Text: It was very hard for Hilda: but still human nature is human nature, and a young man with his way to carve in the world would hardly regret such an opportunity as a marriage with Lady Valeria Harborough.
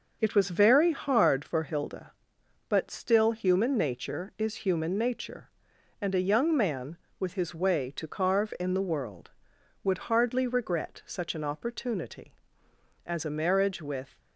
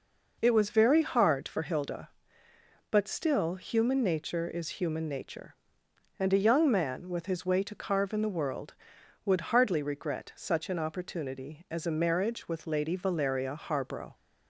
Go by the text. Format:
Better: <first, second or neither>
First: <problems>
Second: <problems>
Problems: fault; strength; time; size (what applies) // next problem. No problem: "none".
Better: second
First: starts louder than the rest; noticeable; until 1.2 s; 6 dB // stops before "Lady Valeria Harborough"; at 14.1 s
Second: none